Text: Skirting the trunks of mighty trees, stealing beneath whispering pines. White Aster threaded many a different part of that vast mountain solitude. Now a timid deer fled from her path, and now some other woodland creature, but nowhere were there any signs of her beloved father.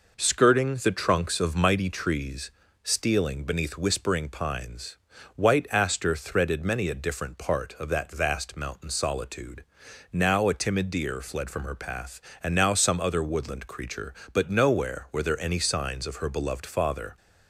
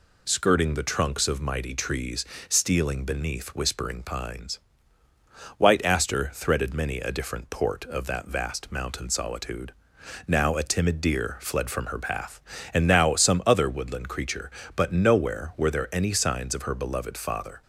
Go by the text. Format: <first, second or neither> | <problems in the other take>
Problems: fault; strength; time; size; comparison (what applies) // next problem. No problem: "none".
first | says "port" for "part"; at 7.4 s